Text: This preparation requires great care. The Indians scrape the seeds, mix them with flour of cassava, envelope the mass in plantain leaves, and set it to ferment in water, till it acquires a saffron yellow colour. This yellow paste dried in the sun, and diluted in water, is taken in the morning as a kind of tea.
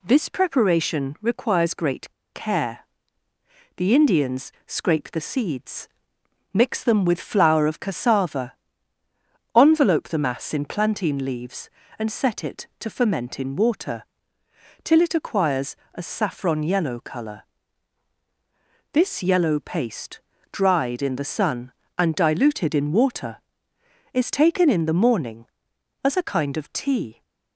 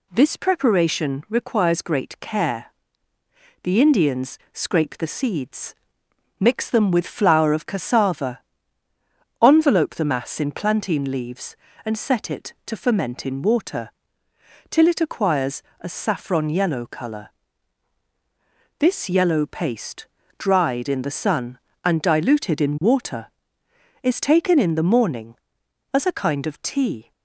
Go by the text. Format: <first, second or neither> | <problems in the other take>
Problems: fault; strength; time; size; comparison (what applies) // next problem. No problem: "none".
second | pauses between "great" and "care"; slight; at 2.1 s; 0.23 s long // pauses between "Indians" and "scrape"; slight; at 4.5 s; 0.16 s long; slight in the second // pauses between "acquires" and "a"; slight; at 15.7 s; 0.20 s long; slight in the second // pauses between "paste" and "dried"; slight; at 20.1 s; 0.32 s long; slight in the second